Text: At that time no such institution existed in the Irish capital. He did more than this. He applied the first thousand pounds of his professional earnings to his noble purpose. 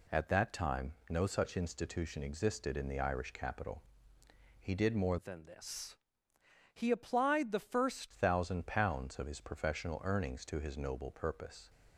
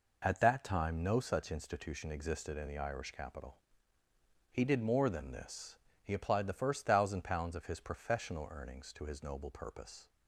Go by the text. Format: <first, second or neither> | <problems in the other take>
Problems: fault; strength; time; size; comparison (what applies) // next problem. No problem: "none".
second | pauses between "time" and "no"; slight; at 0.9 s; 0.16 s long // changes voice from "than" to "first"; from 5.1 to 8.1 s; 3.0 s long